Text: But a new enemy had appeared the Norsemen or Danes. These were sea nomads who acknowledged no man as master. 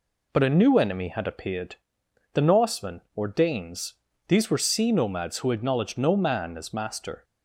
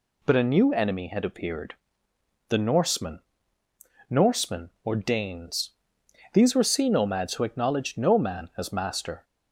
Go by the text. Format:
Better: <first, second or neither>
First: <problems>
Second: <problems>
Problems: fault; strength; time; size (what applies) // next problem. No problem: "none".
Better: first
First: pauses between "appeared" and "the"; noticeable; at 1.7 s; 0.58 s long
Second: pauses between "appeared" and "the"; noticeable; at 1.7 s; 0.76 s long // says "Norsemen" twice; at 4.0 s